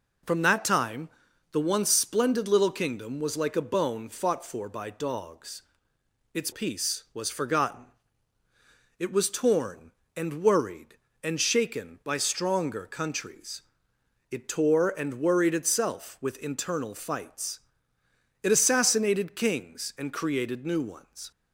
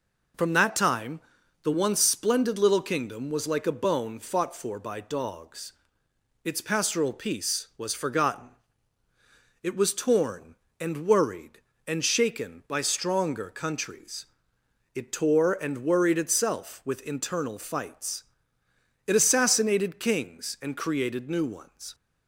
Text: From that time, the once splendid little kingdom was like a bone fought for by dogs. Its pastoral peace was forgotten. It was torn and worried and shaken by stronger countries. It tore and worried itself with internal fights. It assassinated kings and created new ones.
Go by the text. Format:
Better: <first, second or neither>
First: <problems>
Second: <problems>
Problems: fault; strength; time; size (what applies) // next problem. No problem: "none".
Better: second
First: skips "pastoral"; at 6.5 s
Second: none